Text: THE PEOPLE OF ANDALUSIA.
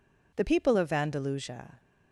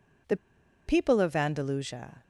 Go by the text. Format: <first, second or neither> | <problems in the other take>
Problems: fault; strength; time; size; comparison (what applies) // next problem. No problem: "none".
first | pauses between "THE" and "PEOPLE"; noticeable; at 0.3 s; 0.50 s long